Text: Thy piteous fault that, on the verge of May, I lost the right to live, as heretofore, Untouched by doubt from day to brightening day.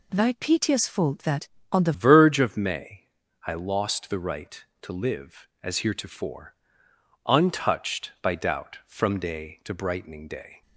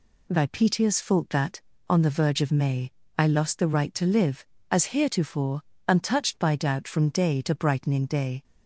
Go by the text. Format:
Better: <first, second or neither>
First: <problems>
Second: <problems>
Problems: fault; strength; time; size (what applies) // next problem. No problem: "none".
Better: second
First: changes voice at "verge"; from 1.9 s on; 8.7 s long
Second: none